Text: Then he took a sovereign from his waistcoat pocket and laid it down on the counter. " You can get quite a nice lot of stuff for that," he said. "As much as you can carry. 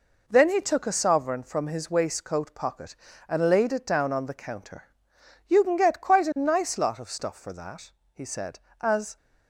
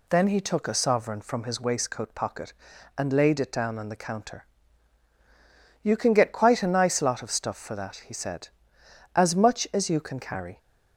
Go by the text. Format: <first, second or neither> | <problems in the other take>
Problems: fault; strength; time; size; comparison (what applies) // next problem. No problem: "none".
second | stops before "much as you can carry"; at 9.1 s